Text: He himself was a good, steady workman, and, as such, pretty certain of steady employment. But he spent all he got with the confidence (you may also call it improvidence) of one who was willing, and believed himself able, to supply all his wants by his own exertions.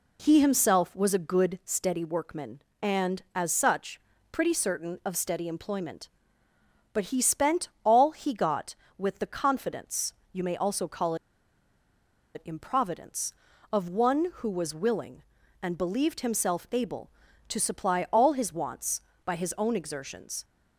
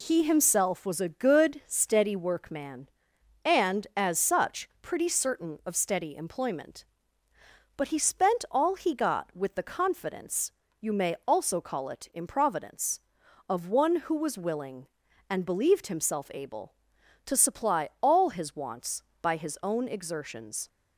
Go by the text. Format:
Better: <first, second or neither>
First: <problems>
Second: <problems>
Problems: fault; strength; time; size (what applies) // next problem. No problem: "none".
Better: second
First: pauses between "spent" and "all"; slight; at 7.6 s; 0.18 s long // pauses between "call" and "it"; at 11.1 s; 1.2 s long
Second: none